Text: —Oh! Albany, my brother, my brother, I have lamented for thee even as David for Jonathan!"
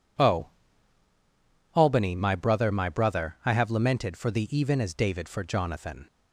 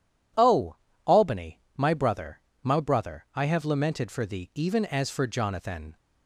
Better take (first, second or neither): first